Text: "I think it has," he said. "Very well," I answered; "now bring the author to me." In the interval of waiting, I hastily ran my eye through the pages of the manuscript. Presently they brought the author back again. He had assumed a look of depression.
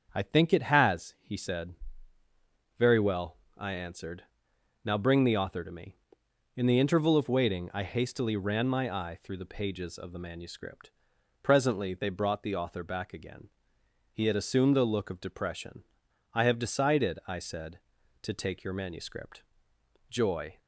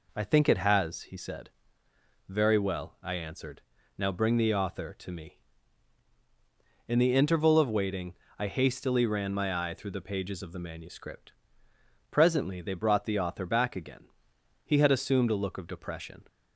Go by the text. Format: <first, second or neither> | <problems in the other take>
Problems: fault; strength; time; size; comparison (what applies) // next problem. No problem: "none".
second | starts louder than the rest; until 1.1 s; 6.5 dB // goes on to say "I have decided I said to take your manuscript Joy"; strong; from 16.3 s on; 4.2 s long